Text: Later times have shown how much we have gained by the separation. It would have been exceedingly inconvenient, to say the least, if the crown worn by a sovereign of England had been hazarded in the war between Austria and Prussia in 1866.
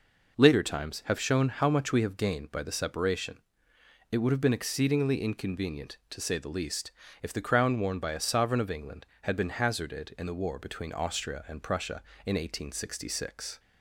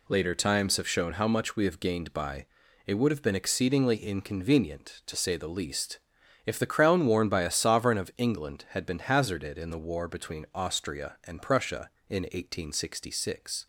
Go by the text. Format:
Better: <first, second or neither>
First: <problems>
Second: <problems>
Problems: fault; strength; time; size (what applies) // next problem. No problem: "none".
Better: first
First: none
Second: skips "the separation"; at 2.6 s